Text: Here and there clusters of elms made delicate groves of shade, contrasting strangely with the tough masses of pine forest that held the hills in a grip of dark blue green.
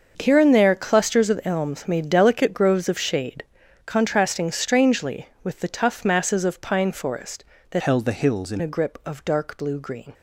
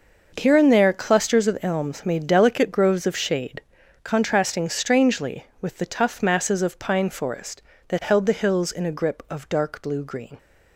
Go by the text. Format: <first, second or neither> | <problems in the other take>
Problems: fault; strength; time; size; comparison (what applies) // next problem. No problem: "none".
second | starts louder than the rest; until 1.1 s; 6.5 dB // changes voice from "held" to "in"; from 7.8 to 8.6 s; 0.8 s long